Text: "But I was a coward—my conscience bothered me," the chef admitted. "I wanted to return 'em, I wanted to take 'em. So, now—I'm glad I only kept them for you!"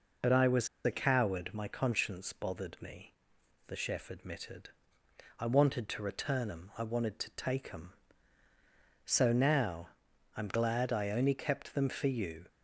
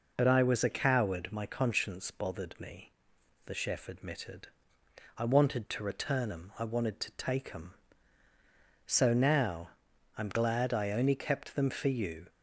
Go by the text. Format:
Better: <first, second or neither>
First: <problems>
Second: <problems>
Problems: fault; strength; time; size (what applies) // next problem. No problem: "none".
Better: second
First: pauses between "was" and "a"; slight; at 0.6 s; 0.17 s long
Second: none